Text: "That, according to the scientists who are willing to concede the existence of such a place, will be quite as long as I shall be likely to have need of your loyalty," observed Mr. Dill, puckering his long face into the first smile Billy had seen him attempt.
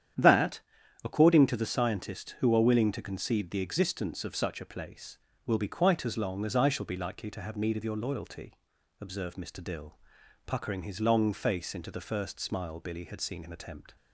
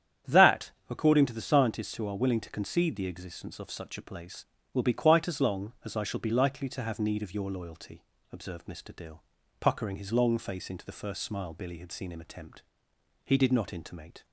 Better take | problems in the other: first | starts louder than the rest; strong; until 1.4 s; 9.5 dB; strong in the first // goes on to say "He did not intimate"; noticeable; from 13.2 s on; 1.0 s long

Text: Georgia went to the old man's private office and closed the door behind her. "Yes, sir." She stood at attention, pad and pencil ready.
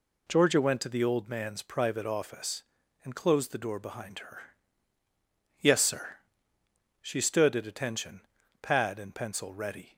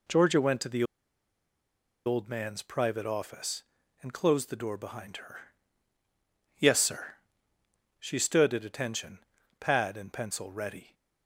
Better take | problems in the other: first | pauses between "the" and "old"; at 0.8 s; 1.2 s long

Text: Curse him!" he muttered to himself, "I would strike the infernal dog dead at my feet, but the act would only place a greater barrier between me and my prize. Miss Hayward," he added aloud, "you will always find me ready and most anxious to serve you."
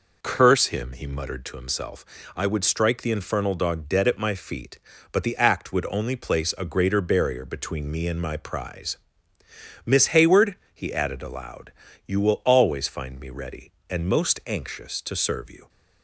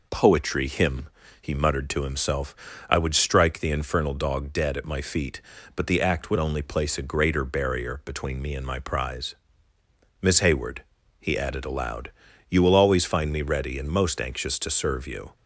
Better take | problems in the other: first | says "Poetry" for "Curse"; at 0.1 s

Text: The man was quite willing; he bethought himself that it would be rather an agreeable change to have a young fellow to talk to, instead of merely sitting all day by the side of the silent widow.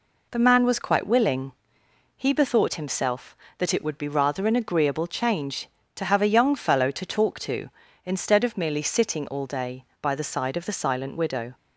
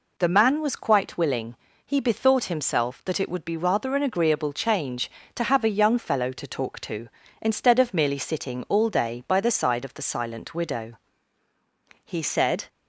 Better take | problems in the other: first | goes on to say "He said"; noticeable; from 12.0 s on; 0.62 s long

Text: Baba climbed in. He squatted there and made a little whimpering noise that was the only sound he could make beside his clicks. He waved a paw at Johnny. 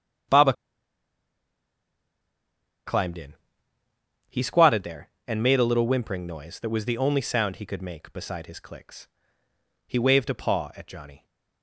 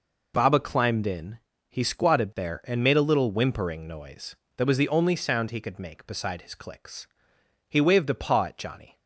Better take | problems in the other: second | starts louder than the rest; until 4.5 s; 7 dB // pauses between "Baba" and "climbed"; strong; at 0.5 s; 2.3 s long

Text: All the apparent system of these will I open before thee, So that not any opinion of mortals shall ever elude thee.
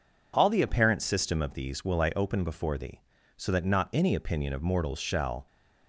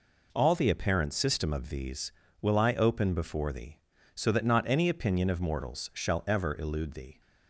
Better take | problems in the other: second | stops before "ever elude thee"; at 5.4 s

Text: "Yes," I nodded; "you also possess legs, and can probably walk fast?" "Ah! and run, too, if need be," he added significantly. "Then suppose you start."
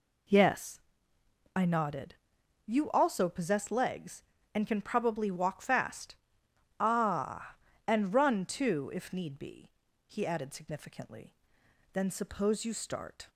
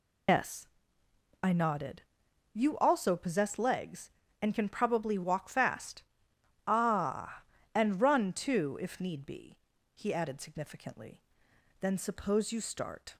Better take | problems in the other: first | loses the start of "Yes"; at 0.2 s; 135 ms

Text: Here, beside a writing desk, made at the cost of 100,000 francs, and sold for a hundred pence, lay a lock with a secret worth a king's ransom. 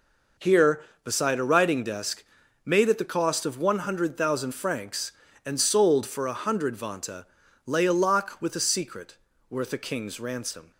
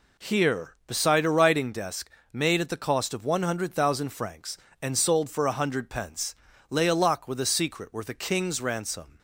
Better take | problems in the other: second | says "vanta" for "pence"; at 6.7 s // pauses between "secret" and "worth"; slight; at 9.1 s; 0.32 s long

